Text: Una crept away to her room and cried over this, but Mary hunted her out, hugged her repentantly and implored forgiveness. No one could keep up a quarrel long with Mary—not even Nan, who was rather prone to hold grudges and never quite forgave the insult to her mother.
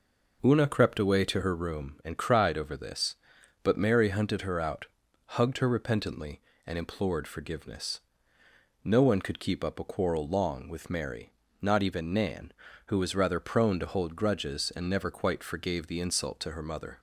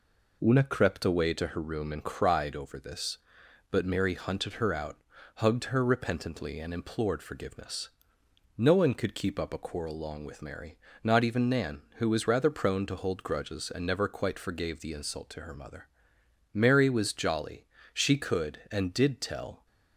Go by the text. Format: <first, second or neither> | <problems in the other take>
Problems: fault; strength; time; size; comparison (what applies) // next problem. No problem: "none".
first | goes on to say "Mary was jolly She could and did tell"; strong; from 16.5 s on; 3.1 s long